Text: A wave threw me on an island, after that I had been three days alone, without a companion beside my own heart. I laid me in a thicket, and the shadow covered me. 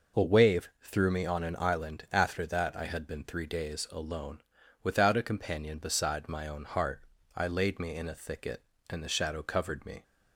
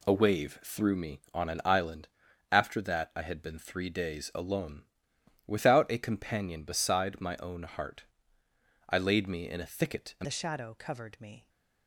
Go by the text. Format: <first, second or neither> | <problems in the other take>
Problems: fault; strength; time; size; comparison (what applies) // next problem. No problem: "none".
first | changes voice at "the"; from 10.2 s on; 1.2 s long